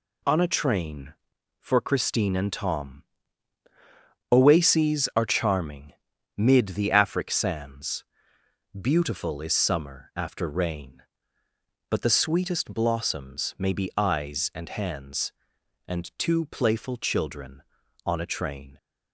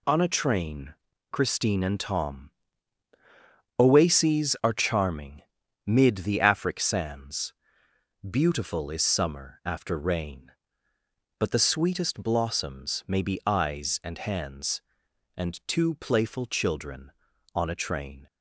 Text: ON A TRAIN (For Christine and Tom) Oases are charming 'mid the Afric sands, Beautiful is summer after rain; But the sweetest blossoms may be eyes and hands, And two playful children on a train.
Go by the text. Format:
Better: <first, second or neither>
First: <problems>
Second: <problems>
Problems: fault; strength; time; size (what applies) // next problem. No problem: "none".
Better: first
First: pauses between "charming" and "mid"; at 5.9 s; 0.44 s long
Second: skips "For"; at 1.1 s // pauses between "charming" and "mid"; at 5.4 s; 0.44 s long